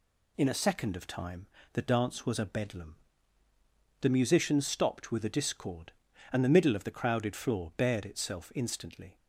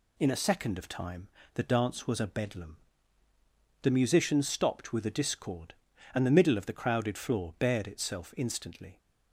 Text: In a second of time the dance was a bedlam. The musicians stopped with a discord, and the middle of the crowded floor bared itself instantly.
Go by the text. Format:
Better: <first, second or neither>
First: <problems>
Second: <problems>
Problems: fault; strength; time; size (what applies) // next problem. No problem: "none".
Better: neither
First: pauses between "time" and "the"; slight; at 1.4 s; 0.28 s long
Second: pauses between "time" and "the"; slight; at 1.2 s; 0.28 s long